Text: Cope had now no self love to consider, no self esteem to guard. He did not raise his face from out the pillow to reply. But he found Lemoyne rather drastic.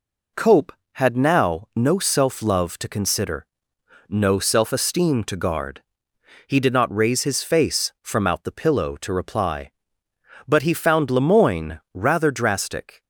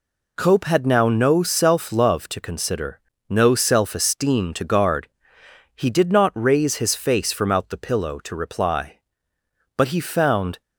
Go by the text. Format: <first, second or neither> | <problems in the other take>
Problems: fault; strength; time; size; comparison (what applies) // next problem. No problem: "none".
first | stops before "Lemoyne rather drastic"; at 10.6 s